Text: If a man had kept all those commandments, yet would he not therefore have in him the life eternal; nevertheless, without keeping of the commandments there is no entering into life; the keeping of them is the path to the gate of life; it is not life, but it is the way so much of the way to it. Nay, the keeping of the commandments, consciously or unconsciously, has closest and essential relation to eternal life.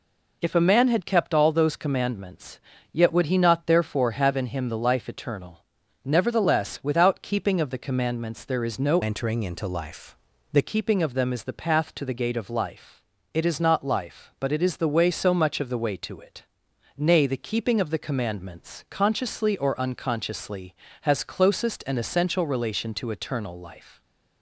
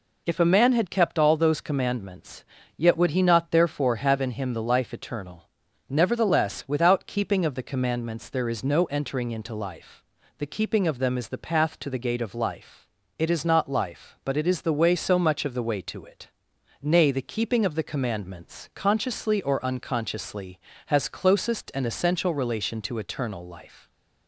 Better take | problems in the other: second | changes voice from "entering" to "the"; from 9.0 to 10.6 s; 1.6 s long

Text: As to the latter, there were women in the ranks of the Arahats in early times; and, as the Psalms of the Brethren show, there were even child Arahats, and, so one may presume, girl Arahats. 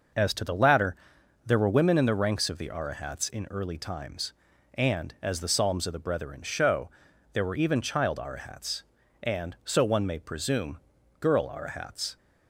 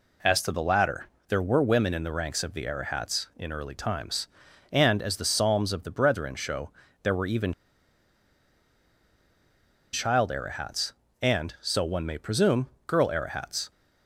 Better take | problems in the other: first | pauses between "even" and "child"; strong; at 7.5 s; 2.3 s long

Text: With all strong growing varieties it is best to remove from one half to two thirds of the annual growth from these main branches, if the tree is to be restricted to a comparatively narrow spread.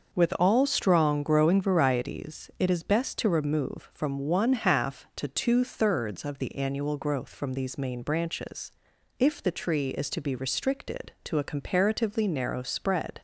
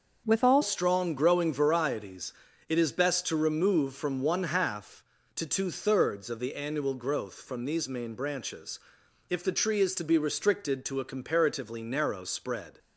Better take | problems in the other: first | starts louder than the rest; noticeable; until 1.2 s; 6 dB // changes voice at "strong"; from 0.6 s on; 12.1 s long // pauses between "varieties" and "it"; slight; at 2.3 s; 0.36 s long

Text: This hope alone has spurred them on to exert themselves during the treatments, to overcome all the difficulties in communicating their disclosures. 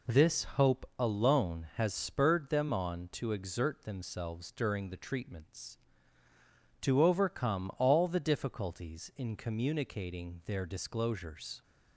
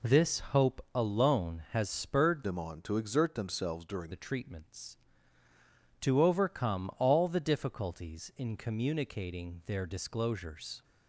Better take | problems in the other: first | changes voice from "them" to "during"; from 2.4 to 4.1 s; 1.7 s long

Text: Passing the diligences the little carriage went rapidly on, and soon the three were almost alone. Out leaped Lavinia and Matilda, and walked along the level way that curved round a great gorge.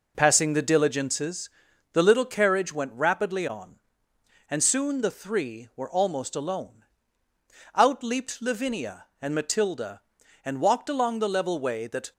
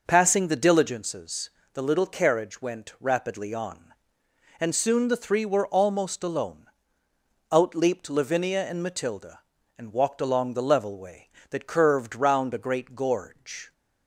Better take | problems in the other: second | pauses between "diligences" and "the"; at 1.4 s; 0.42 s long; slight in the second // stops before "curved round a great gorge"; at 12.1 s

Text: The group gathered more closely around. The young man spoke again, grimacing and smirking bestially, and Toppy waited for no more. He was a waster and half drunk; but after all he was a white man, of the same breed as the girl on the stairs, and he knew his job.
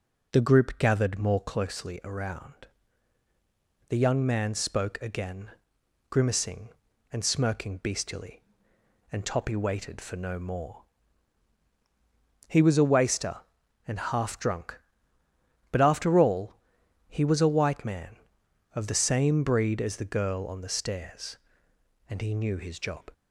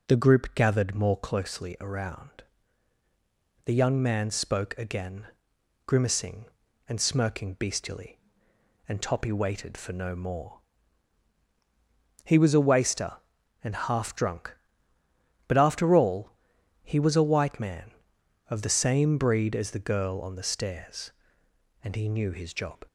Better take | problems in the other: neither | pauses between "all" and "he"; noticeable; the same in both

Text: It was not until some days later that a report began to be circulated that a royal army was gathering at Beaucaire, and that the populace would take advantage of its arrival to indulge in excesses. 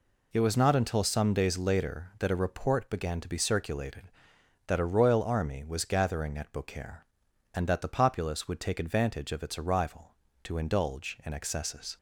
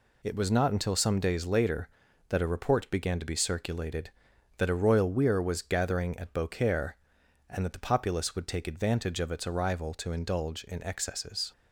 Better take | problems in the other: first | says "weir" for "army"; at 5.0 s

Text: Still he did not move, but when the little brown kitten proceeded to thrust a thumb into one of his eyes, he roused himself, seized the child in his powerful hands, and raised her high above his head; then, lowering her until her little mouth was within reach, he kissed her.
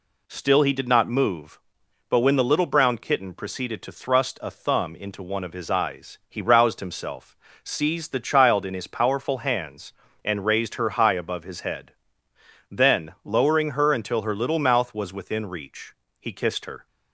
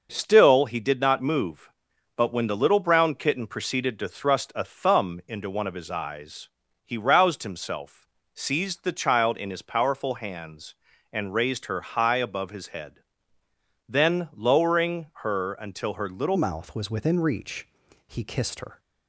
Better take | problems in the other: first | pauses between "lowering" and "her"; slight; at 15.0 s; 0.16 s long // changes voice at "mouth"; from 16.3 s on; 2.4 s long

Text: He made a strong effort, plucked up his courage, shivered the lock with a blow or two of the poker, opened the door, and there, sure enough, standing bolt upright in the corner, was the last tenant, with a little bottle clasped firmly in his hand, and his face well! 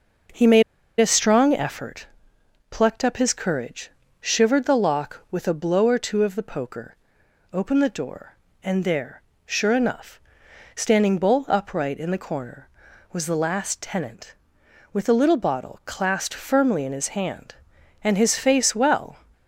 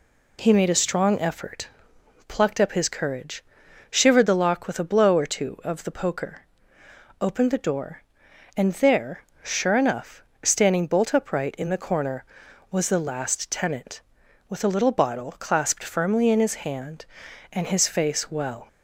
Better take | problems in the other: second | pauses between "made" and "a"; at 0.6 s; 0.37 s long

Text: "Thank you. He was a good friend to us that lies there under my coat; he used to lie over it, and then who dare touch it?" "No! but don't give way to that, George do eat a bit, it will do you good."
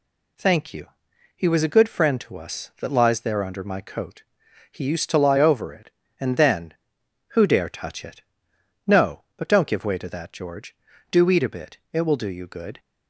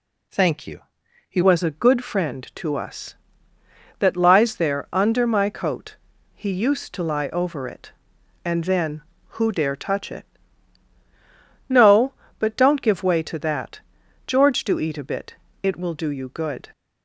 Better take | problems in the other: first | changes voice at "was"; from 1.4 s on; 15.2 s long

